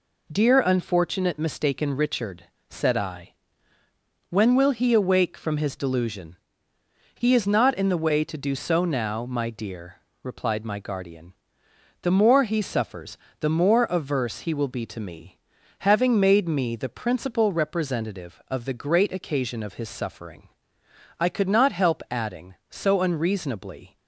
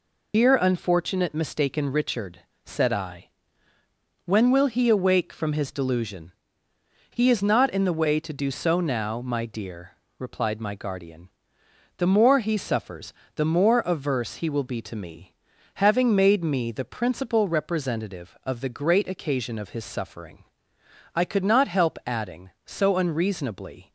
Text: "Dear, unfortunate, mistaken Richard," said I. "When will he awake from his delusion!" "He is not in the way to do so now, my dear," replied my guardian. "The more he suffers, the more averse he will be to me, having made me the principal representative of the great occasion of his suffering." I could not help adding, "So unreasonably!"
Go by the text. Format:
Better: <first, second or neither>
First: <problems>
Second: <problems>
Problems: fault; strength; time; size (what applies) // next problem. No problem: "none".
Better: first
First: none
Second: loses the start of "Dear"; at 0.3 s; 95 ms